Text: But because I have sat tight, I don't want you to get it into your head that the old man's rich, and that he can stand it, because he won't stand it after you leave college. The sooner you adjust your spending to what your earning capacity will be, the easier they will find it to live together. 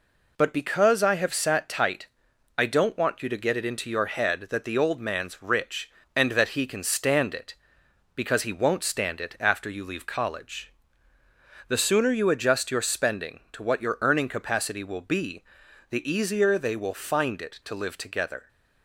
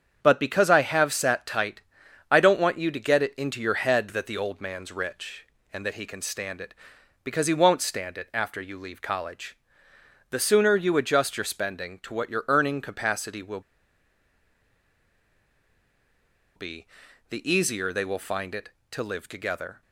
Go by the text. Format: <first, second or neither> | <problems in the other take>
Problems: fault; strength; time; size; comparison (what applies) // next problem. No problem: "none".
first | starts louder than the rest; strong; until 1.2 s; 8 dB // pauses between "will" and "be"; strong; at 13.6 s; 2.9 s long